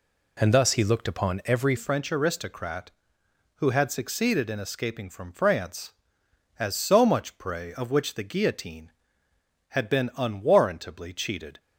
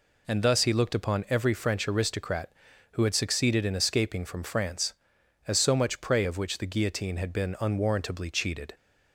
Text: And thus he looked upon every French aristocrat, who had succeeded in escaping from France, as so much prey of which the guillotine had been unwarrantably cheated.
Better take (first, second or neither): second